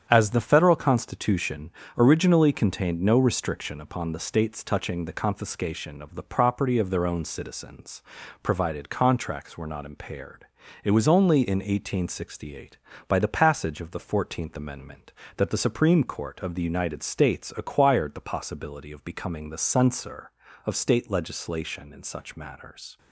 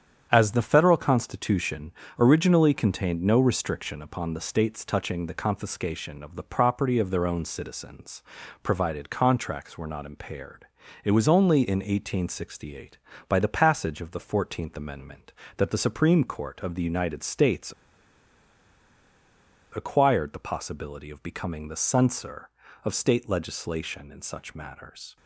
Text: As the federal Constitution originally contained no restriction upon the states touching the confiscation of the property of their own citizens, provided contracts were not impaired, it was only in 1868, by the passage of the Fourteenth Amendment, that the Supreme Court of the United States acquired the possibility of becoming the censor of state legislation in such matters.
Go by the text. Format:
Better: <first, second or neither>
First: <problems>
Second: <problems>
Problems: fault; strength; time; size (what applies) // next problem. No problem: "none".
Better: first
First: starts louder than the rest; strong; until 1.1 s; 8.5 dB // pauses between "Constitution" and "originally"; slight; at 1.7 s; 0.26 s long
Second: starts louder than the rest; strong; until 1.3 s; 8.5 dB // pauses between "Constitution" and "originally"; slight; at 1.9 s; 0.26 s long // pauses between "States" and "acquired"; strong; at 17.7 s; 2.0 s long